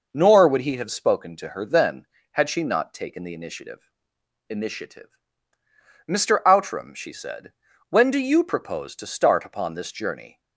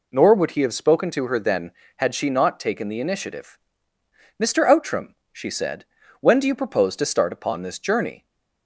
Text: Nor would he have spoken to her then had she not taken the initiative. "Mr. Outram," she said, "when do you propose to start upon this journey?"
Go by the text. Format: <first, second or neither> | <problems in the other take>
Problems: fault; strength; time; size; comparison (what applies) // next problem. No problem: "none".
second | says "initiative" twice; at 4.4 s